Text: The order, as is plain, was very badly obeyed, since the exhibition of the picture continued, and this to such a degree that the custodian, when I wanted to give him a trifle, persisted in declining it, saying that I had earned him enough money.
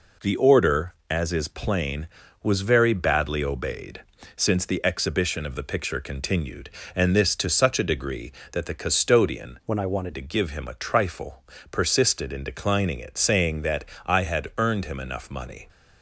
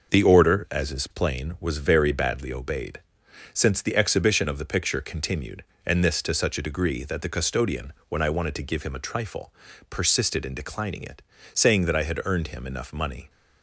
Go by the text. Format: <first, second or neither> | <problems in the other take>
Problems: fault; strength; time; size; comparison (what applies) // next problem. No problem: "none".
second | changes voice from "when" to "wanted"; from 9.6 to 10.1 s; 0.5 s long // pauses between "that" and "I"; slight; at 13.8 s; 0.18 s long